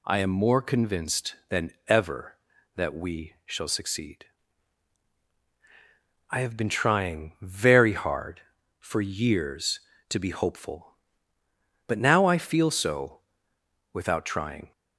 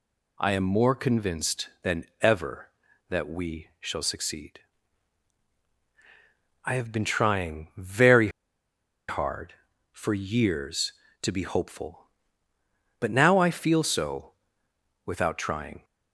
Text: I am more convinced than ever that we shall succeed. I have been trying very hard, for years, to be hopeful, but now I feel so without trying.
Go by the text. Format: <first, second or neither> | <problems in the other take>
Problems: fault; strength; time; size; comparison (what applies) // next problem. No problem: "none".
first | pauses between "than" and "ever"; slight; at 2.0 s; 0.16 s long; slight in the first // pauses between "very" and "hard"; noticeable; at 8.2 s; 0.81 s long // pauses between "so" and "without"; noticeable; at 14.3 s; 0.74 s long; noticeable in the first